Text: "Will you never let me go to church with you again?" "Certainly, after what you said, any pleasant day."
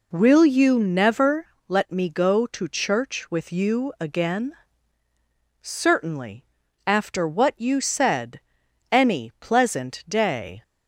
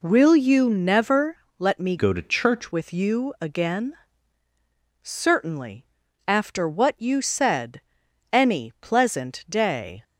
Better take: first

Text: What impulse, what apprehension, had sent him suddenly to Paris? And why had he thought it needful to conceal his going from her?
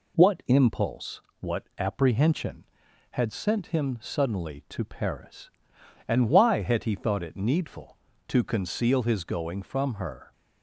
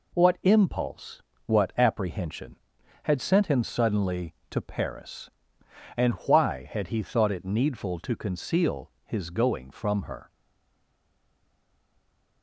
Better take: first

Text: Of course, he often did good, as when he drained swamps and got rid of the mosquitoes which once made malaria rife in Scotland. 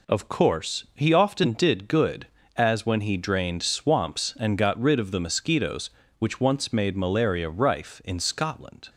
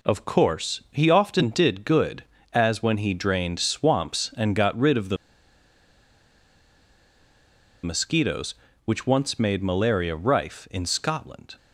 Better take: first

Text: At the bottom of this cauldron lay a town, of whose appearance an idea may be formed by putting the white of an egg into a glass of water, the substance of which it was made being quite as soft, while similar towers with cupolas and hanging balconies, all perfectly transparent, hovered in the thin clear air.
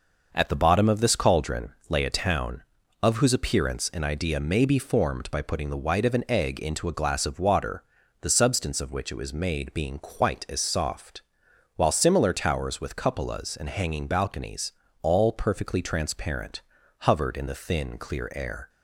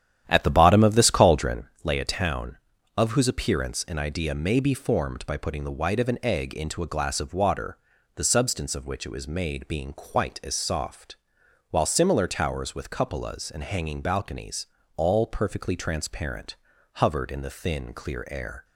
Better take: first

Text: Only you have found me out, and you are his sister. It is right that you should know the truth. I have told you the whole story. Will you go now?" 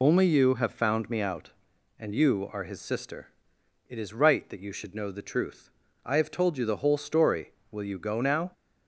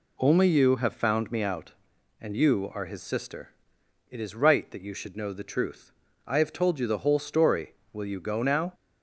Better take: second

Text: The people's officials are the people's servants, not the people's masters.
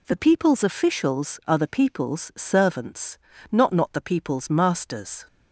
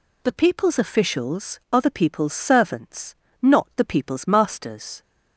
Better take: second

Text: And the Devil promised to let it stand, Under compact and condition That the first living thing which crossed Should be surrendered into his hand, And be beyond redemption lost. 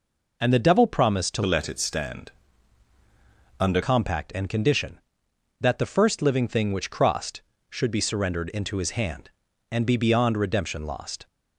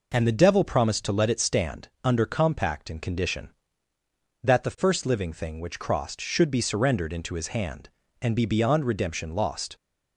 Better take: second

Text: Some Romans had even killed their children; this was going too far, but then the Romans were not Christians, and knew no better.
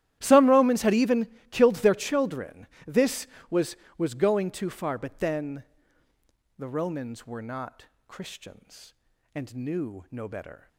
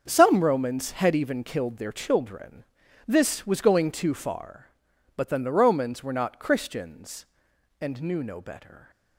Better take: second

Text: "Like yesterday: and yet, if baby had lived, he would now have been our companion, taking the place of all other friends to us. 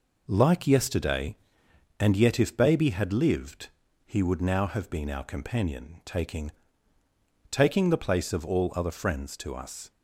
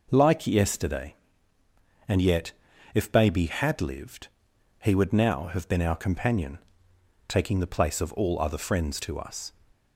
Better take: second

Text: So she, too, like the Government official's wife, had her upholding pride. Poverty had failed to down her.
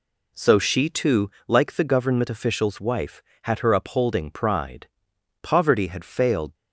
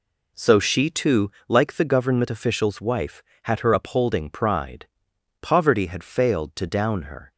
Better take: second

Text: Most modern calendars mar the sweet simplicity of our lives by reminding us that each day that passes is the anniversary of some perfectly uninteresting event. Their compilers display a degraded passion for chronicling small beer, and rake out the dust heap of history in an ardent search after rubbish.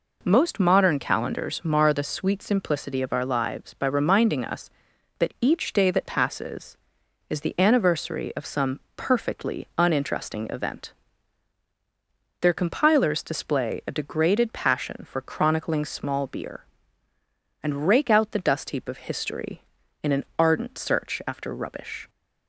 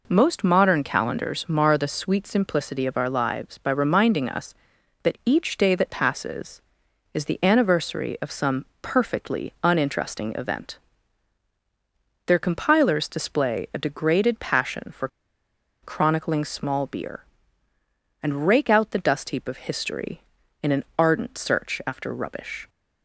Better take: first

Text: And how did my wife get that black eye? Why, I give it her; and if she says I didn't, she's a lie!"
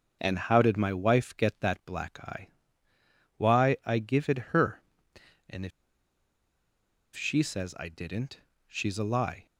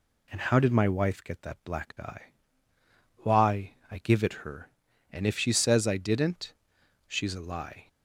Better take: second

